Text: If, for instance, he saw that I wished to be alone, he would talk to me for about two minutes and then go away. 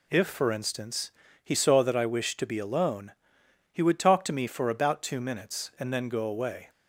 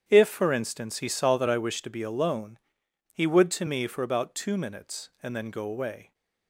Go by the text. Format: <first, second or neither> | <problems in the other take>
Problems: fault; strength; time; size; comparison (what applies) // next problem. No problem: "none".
first | starts louder than the rest; strong; until 1.0 s; 8.5 dB // skips "talk"; at 3.5 s